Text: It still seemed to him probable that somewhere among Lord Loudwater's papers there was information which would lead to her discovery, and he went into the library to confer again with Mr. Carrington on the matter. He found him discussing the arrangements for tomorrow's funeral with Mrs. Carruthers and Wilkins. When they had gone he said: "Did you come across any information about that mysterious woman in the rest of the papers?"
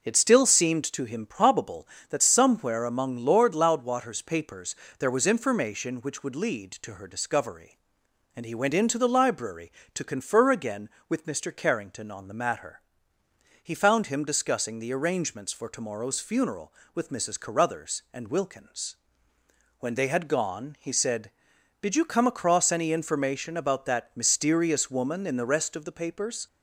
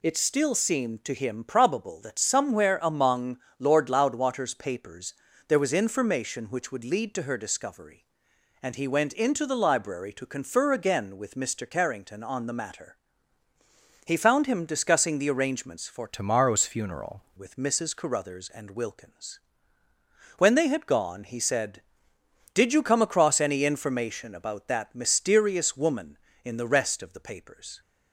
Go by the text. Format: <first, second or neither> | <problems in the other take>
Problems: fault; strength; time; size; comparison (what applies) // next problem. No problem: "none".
first | pauses between "among" and "Lord"; slight; at 3.3 s; 0.20 s long // pauses between "papers" and "there"; slight; at 5.1 s; 0.36 s long; slight in the first // changes voice from "tomorrow's" to "funeral"; from 16.0 to 17.2 s; 1.2 s long